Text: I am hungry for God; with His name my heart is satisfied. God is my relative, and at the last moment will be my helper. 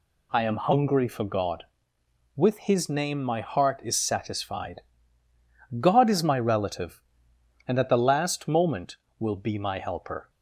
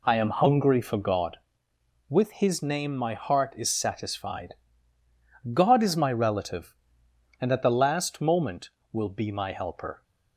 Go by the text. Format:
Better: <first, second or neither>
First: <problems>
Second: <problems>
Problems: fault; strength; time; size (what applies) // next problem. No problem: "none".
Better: first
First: none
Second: starts louder than the rest; slight; until 1.4 s; 2.5 dB